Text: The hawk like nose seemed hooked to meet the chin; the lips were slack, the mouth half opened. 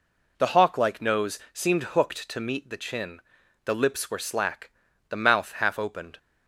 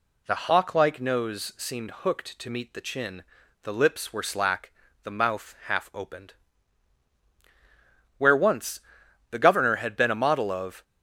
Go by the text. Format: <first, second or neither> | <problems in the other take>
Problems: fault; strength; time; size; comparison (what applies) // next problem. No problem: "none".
first | goes on to say "Where once the Governor had been a model of"; strong; from 8.1 s on; 2.6 s long